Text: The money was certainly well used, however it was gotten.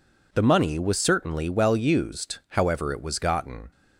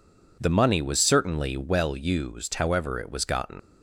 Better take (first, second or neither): first